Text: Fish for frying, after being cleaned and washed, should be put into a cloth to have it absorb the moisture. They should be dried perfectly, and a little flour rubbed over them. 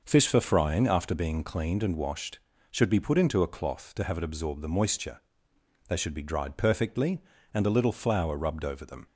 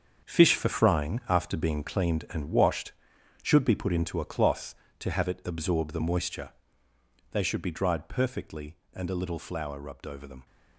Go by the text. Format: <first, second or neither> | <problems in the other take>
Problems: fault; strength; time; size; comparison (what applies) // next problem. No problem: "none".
first | gets quieter; strong; throughout; 10.5 dB